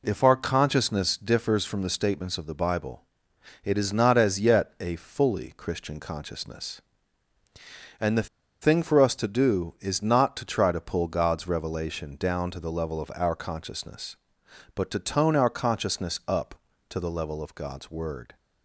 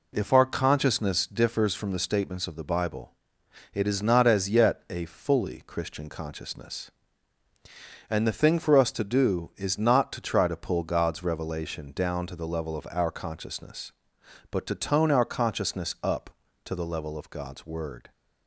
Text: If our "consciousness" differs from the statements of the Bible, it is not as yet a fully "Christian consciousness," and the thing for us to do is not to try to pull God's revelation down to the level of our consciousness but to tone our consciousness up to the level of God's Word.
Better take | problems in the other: second | pauses between "the" and "thing"; slight; at 8.2 s; 0.33 s long

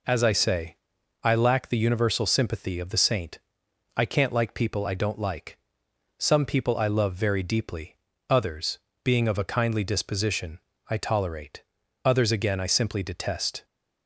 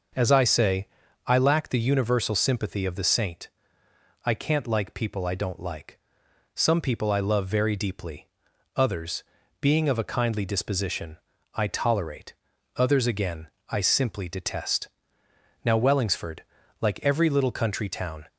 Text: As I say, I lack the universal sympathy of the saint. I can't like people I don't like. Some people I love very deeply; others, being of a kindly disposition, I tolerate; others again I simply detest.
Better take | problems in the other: first | starts louder than the rest; until 1.5 s; 6.5 dB // pauses between "again" and "I"; slight; at 13.4 s; 0.22 s long // goes on to say "Now Wellingsford like every little country town"; strong; from 15.6 s on; 2.6 s long

